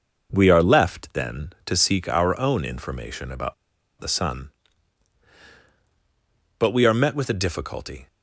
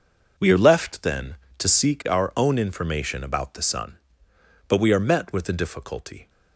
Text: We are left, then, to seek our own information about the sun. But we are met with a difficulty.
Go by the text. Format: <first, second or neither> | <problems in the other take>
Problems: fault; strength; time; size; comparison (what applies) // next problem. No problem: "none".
second | pauses between "about" and "the"; noticeable; at 3.5 s; 0.46 s long